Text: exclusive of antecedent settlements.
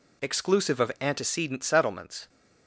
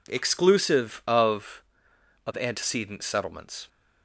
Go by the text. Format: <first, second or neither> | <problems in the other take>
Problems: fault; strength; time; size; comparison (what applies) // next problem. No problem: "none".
first | says "of" twice; at 2.2 s